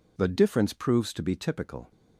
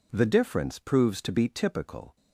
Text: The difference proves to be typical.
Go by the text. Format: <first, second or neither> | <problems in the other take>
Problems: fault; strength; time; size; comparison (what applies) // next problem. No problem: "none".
neither | none